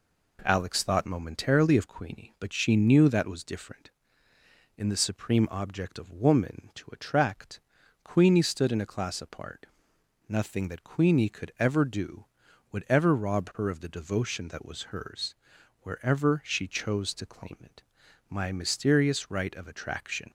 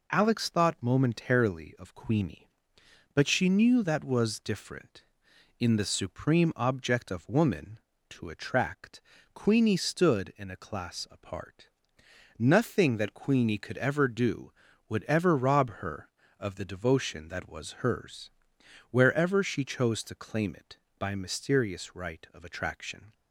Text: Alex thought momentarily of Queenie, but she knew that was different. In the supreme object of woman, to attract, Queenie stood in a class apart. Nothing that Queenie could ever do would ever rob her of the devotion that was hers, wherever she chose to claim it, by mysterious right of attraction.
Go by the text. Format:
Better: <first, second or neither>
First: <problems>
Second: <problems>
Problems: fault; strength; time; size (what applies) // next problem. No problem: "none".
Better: second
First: says "my" for "by"; at 18.2 s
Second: none